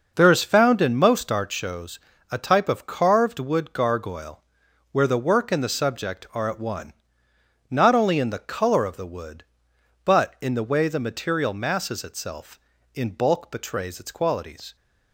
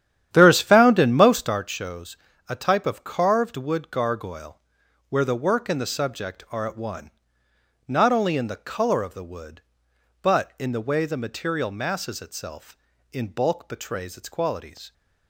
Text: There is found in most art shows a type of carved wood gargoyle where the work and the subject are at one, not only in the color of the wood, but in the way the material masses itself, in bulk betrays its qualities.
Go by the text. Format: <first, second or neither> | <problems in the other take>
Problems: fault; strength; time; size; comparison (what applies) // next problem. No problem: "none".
first | starts louder than the rest; strong; until 1.6 s; 10.5 dB // pauses between "shows" and "a"; slight; at 2.1 s; 0.32 s long; slight in the first // pauses between "gargoyle" and "where"; noticeable; at 4.6 s; 0.48 s long; noticeable in the first